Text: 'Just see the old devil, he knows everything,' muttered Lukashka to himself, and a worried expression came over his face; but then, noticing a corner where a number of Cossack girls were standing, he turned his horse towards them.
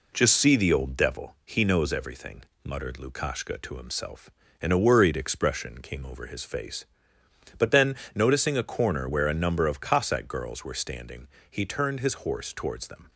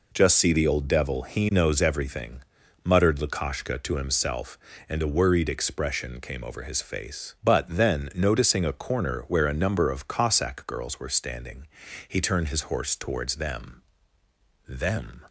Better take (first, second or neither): first